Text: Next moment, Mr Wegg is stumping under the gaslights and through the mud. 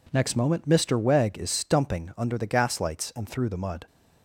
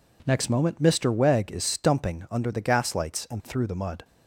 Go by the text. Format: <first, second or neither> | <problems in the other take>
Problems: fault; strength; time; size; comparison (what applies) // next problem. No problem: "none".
neither | none